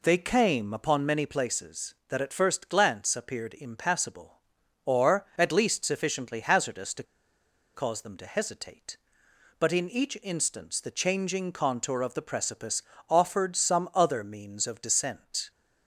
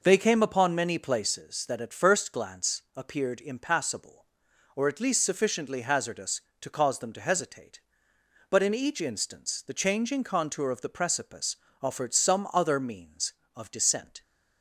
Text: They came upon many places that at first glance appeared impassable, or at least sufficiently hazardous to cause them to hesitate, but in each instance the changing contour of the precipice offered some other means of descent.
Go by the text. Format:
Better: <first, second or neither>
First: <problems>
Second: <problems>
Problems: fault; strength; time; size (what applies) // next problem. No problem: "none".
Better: second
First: pauses between "to" and "cause"; noticeable; at 7.0 s; 0.70 s long // pauses between "precipice" and "offered"; slight; at 12.8 s; 0.26 s long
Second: pauses between "precipice" and "offered"; slight; at 11.5 s; 0.24 s long